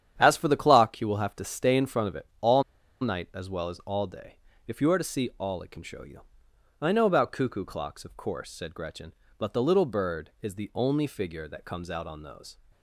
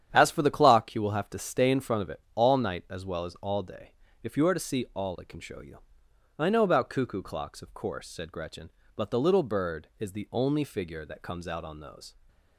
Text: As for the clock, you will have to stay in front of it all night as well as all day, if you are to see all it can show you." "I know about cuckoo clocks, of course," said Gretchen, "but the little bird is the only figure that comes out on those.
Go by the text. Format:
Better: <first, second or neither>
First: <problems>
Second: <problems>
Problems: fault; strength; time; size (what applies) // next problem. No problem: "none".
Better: second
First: starts louder than the rest; strong; until 1.1 s; 9.5 dB // pauses between "it" and "all"; slight; at 2.2 s; 0.16 s long // pauses between "all" and "night"; at 2.6 s; 0.38 s long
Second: starts louder than the rest; strong; until 1.1 s; 9.5 dB // pauses between "it" and "all"; slight; at 2.1 s; 0.16 s long